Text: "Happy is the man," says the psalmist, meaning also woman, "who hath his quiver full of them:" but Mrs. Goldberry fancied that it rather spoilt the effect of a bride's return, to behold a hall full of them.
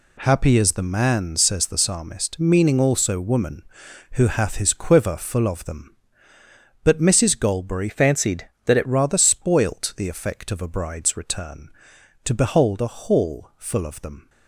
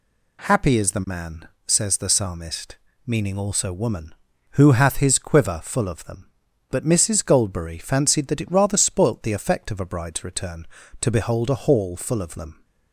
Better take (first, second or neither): second